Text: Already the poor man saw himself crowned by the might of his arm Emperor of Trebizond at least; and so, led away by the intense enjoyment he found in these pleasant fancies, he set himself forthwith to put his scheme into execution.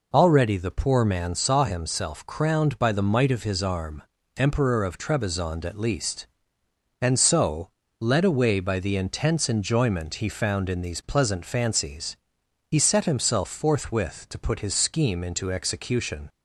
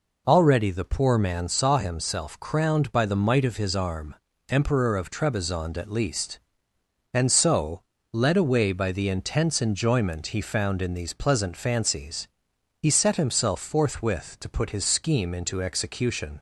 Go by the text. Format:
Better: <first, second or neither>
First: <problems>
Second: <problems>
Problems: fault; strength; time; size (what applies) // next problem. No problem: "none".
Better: neither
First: pauses between "arm" and "Emperor"; slight; at 4.0 s; 0.32 s long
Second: pauses between "arm" and "Emperor"; slight; at 4.1 s; 0.32 s long